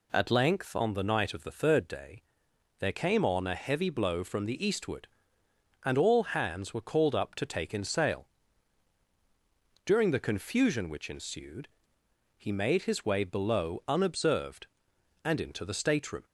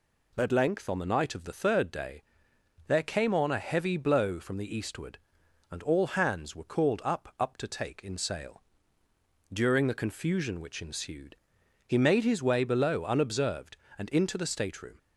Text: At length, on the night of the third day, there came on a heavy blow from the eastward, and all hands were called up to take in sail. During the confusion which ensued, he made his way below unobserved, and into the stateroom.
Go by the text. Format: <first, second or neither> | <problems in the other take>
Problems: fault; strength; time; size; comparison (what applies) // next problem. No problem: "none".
first | says "up" twice; at 7.3 s